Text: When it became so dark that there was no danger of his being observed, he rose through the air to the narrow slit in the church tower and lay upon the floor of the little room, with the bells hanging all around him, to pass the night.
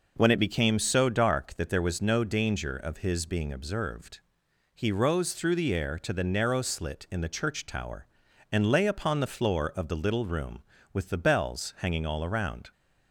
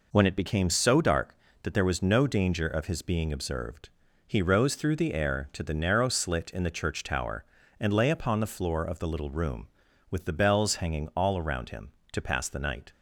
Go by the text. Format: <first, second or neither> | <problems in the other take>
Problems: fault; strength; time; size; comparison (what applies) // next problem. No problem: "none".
second | stops before "him to pass the night"; at 12.7 s